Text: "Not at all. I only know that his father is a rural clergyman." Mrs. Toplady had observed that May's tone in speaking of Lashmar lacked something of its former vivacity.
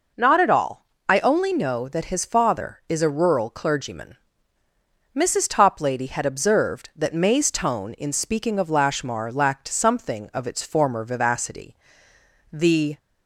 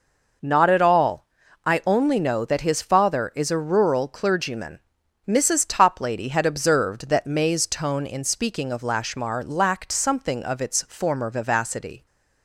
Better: second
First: goes on to say "The"; slight; from 12.5 s on; 0.46 s long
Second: none

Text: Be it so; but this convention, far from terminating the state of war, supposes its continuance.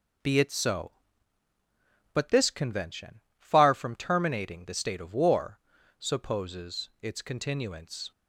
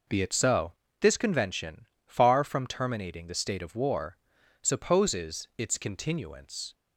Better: first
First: none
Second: skips "but"; at 0.8 s

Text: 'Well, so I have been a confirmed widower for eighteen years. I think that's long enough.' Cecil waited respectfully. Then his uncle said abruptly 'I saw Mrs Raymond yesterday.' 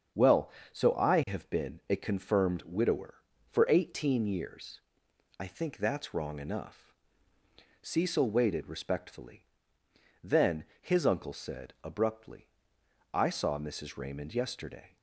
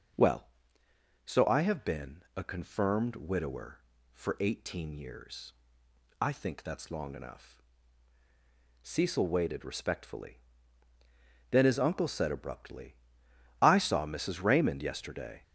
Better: second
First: starts louder than the rest; strong; until 1.4 s; 7 dB // says "wrong" for "long"; at 6.1 s // pauses between "Then" and "his"; slight; at 10.6 s; 0.16 s long // pauses between "abruptly" and "I"; noticeable; at 12.4 s; 0.64 s long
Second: starts louder than the rest; noticeable; until 1.9 s; 6 dB // pauses between "abruptly" and "I"; noticeable; at 12.9 s; 0.68 s long

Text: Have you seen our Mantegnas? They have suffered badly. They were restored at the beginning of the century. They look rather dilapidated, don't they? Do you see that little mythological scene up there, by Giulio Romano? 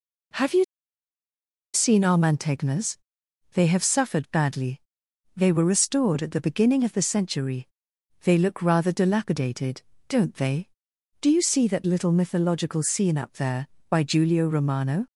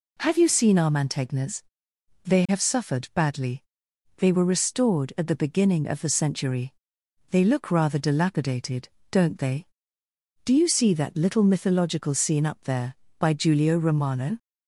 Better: second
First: pauses between "you" and "seen"; at 0.6 s; 1.1 s long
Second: none

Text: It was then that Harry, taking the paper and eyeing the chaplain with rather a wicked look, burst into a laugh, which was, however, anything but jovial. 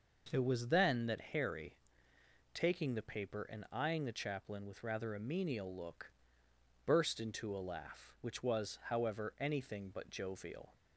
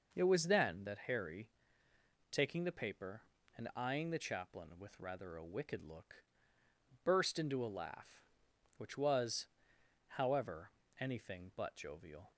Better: second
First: says "menial" for "wicked"; at 5.1 s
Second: none

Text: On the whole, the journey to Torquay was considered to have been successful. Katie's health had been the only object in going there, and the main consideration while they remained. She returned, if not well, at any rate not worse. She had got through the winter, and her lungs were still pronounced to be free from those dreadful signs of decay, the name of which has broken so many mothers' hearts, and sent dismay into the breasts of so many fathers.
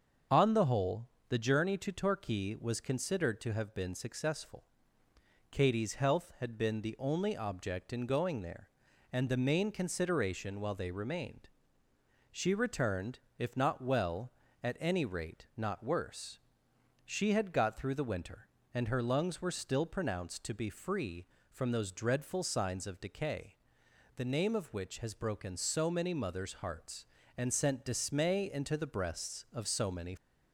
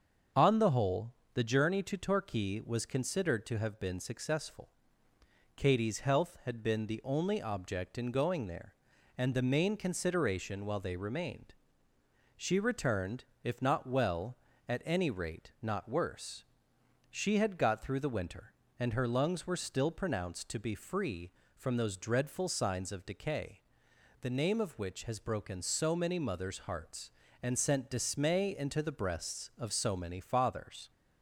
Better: second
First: starts louder than the rest; until 1.5 s; 7 dB // stops before "fathers"; at 30.1 s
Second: starts louder than the rest; until 1.5 s; 7 dB

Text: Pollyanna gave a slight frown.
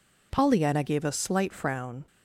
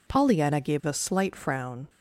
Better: neither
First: none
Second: none

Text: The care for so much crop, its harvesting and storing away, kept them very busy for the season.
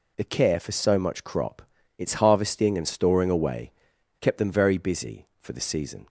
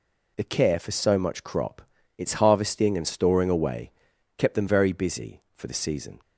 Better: neither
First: none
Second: none

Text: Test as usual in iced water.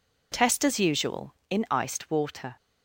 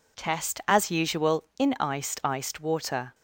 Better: first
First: none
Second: says "iced" twice; at 2.2 s

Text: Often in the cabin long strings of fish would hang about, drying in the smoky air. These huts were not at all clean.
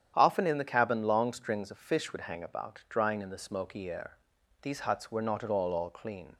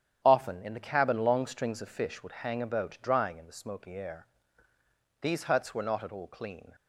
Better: second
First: starts louder than the rest; strong; until 1.1 s; 9.5 dB // says "all" twice; at 5.7 s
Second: starts louder than the rest; strong; until 1.2 s; 9.5 dB

